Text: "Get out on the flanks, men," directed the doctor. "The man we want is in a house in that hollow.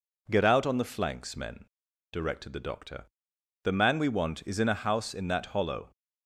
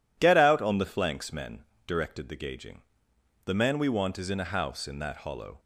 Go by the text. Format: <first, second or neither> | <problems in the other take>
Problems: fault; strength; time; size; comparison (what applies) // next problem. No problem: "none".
first | says "gauging" for "doctor"; at 2.3 s